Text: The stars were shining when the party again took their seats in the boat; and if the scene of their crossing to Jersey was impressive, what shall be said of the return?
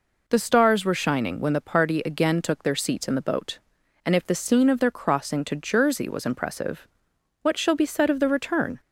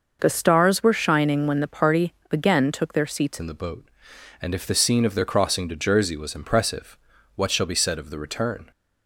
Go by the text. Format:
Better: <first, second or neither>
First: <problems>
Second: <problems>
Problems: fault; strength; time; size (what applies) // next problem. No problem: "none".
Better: first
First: none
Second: pauses between "party" and "again"; slight; at 2.1 s; 0.18 s long // changes voice at "in"; from 3.4 s on; 5.3 s long